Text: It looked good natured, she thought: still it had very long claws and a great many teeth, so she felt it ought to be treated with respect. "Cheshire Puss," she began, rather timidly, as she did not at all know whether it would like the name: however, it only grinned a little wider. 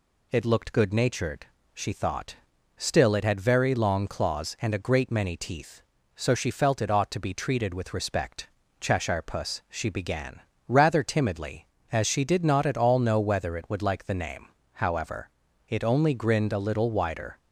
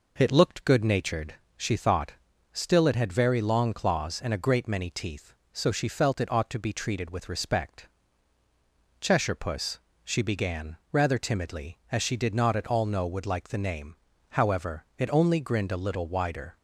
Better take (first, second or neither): first